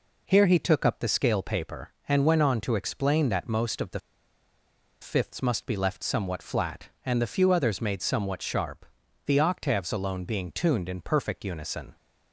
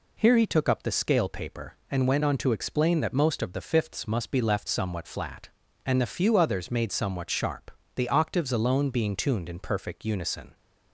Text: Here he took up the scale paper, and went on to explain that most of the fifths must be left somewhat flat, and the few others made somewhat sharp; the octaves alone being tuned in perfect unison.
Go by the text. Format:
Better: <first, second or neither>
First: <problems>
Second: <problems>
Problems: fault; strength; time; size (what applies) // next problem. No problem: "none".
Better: second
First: pauses between "the" and "fifths"; at 4.0 s; 1.0 s long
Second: none